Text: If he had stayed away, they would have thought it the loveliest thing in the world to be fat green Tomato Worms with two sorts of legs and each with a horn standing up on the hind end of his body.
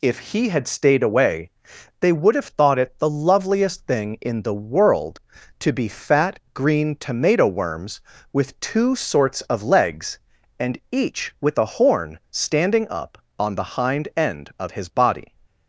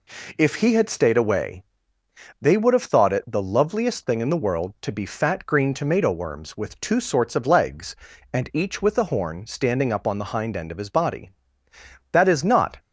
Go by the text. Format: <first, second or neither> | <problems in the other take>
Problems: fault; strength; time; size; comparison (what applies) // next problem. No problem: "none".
first | goes on to say "That is not"; noticeable; from 12.1 s on; 0.66 s long